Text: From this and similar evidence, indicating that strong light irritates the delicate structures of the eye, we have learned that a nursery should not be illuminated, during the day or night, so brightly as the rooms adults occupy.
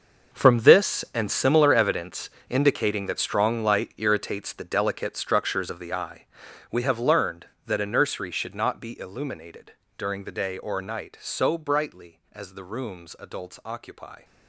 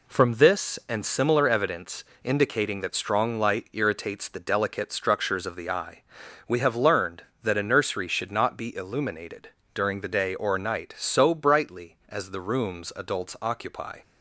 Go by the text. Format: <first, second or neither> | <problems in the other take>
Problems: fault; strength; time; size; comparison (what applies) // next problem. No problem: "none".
second | gets quieter; strong; throughout; 14.5 dB